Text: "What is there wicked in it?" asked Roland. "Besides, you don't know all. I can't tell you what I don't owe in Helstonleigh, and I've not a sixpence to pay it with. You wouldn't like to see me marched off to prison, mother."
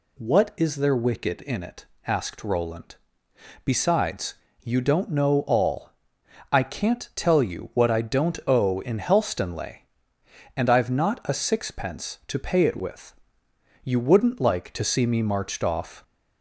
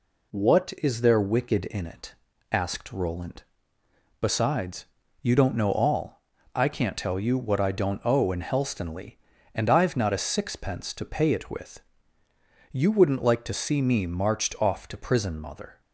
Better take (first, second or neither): second